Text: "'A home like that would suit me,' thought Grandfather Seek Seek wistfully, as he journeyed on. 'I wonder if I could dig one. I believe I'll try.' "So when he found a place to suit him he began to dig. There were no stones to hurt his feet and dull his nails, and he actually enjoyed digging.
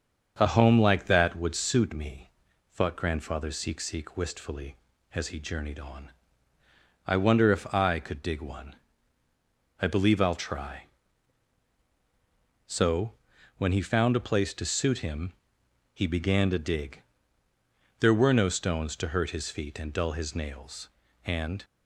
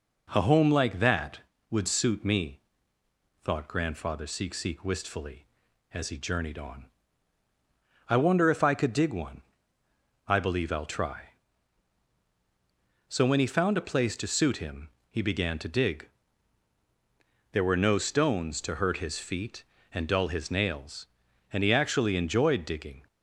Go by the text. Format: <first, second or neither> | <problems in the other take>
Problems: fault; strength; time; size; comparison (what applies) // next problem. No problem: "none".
second | starts louder than the rest; until 1.3 s; 6.5 dB // pauses between "So" and "when"; noticeable; at 13.1 s; 0.46 s long // pauses between "him" and "he"; noticeable; at 15.3 s; 0.60 s long; slight in the second // stops before "he actually enjoyed digging"; at 21.6 s